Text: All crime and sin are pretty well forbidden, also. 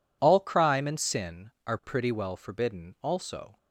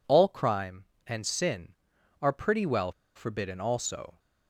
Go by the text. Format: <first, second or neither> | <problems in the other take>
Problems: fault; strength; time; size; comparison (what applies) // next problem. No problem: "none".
first | pauses between "well" and "forbidden"; slight; at 2.9 s; 0.23 s long